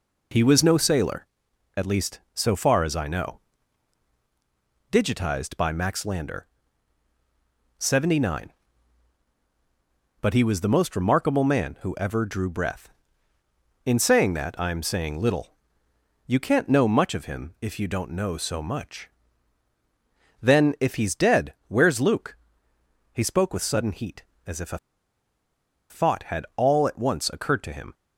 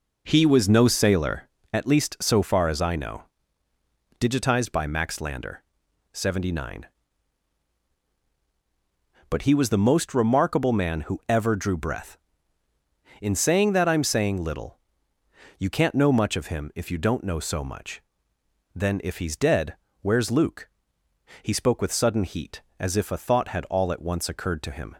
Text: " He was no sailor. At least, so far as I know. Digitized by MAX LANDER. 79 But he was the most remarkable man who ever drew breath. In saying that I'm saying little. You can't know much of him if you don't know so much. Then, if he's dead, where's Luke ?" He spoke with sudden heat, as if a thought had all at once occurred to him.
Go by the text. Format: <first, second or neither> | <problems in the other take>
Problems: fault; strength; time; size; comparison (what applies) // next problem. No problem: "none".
second | pauses between "a" and "thought"; at 24.7 s; 1.1 s long